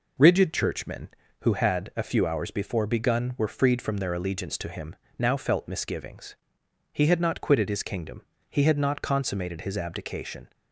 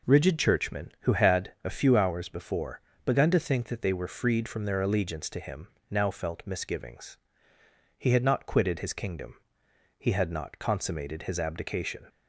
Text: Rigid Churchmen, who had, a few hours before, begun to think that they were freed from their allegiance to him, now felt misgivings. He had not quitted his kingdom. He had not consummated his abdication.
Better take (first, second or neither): second